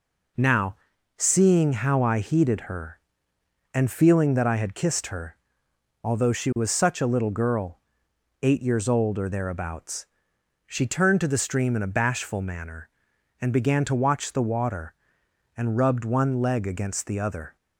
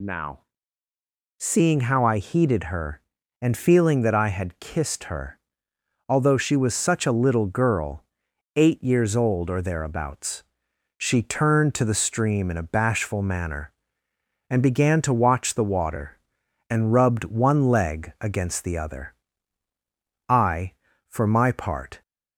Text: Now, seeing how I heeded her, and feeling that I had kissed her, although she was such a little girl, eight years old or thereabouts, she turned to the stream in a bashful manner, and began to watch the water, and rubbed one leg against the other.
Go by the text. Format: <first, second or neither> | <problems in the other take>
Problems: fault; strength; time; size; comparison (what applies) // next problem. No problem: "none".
first | goes on to say "I for my part"; strong; from 20.2 s on; 1.7 s long